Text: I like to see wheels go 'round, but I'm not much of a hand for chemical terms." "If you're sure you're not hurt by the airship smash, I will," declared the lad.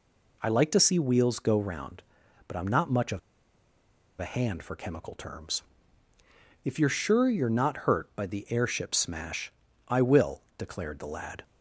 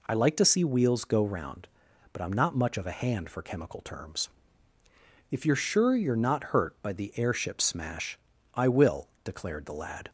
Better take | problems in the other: second | pauses between "of" and "a"; at 3.1 s; 0.99 s long

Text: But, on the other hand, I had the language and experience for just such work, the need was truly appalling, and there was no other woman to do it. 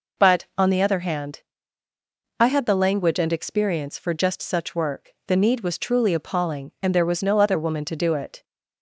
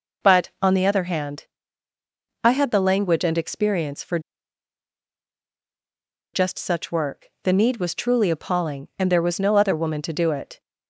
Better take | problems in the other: first | pauses between "for" and "just"; strong; at 4.1 s; 2.1 s long

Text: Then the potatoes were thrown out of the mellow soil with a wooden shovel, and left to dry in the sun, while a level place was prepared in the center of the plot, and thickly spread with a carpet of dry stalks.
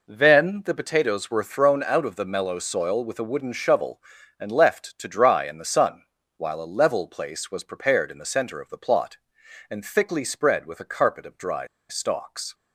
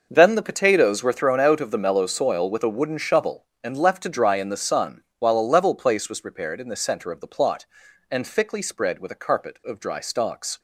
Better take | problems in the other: second | pauses between "dry" and "stalks"; slight; at 11.6 s; 0.23 s long

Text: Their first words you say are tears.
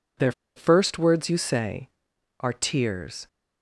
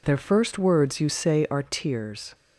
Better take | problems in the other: second | pauses between "Their" and "first"; slight; at 0.3 s; 0.24 s long

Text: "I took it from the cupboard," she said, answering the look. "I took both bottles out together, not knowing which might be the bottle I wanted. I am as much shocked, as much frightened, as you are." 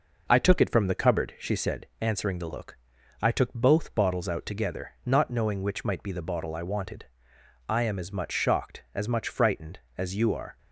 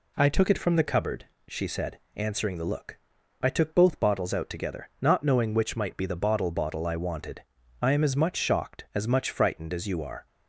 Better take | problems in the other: first | says "bottle" twice; at 6.5 s

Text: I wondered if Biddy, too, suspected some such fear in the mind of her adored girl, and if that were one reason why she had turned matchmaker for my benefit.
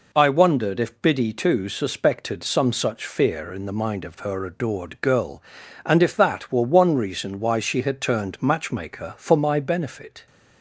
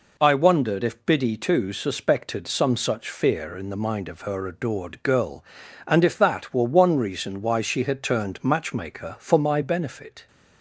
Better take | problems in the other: neither | none

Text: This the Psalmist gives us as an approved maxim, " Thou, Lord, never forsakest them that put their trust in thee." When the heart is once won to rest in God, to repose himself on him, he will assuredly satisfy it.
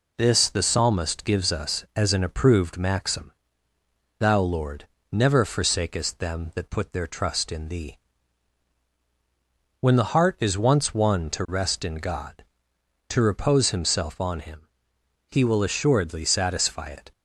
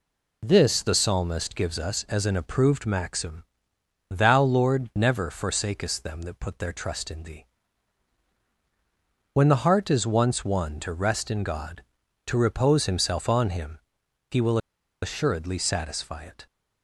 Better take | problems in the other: first | pauses between "will" and "assuredly"; at 14.5 s; 0.44 s long

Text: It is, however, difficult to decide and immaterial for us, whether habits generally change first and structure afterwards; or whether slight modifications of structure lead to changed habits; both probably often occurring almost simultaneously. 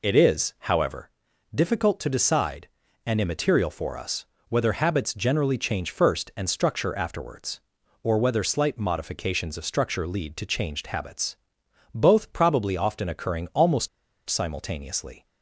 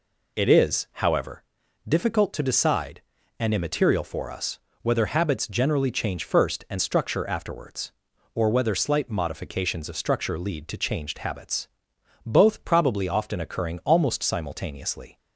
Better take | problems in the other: second | pauses between "almost" and "simultaneously"; at 13.8 s; 0.40 s long

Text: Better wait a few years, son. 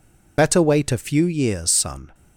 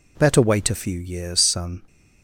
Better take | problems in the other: second | loses the start of "Better"; at 0.3 s; 40 ms

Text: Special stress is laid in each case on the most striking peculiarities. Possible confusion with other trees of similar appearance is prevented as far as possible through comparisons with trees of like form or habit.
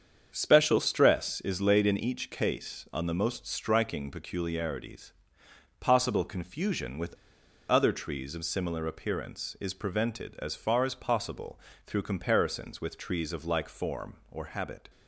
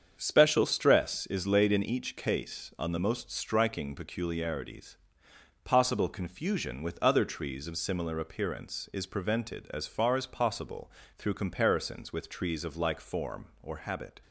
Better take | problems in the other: second | starts louder than the rest; strong; until 1.3 s; 7 dB; strong in the second // pauses between "with" and "other"; noticeable; at 7.1 s; 0.55 s long // pauses between "possible" and "through"; slight; at 11.5 s; 0.28 s long; slight in the second

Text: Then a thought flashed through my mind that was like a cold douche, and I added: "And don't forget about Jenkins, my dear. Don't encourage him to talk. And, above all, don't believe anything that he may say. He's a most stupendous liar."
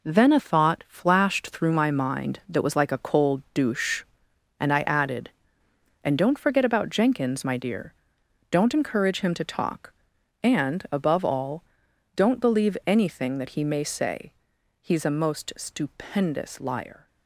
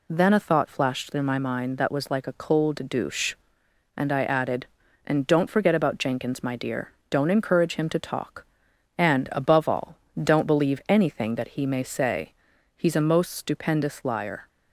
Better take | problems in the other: second | gets quieter; strong; throughout; 7.5 dB

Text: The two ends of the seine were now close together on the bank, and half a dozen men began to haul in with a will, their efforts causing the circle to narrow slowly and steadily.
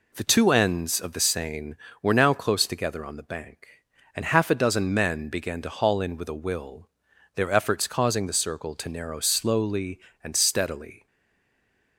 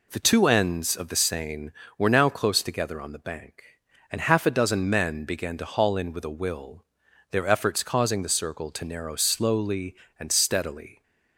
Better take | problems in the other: second | stays silent after the last word; from 11.0 s on; 0.9 s long

